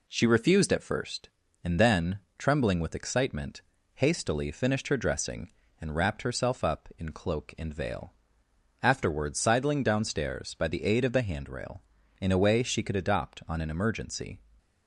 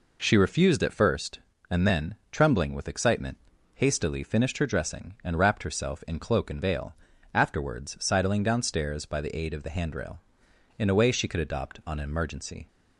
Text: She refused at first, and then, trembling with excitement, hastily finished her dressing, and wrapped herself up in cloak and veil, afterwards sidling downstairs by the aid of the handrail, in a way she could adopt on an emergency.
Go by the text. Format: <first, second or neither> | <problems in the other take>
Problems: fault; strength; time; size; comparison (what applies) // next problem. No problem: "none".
first | skips "up"; at 6.0 s